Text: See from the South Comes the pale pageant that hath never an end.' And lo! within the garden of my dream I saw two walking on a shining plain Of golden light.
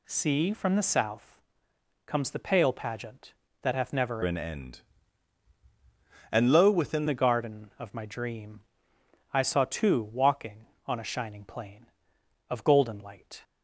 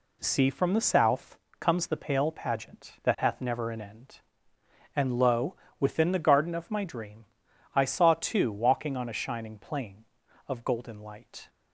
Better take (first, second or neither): second